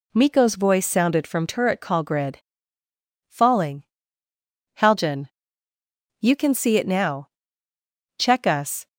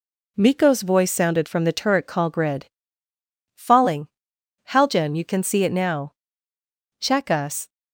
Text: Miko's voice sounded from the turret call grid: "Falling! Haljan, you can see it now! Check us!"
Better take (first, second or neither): second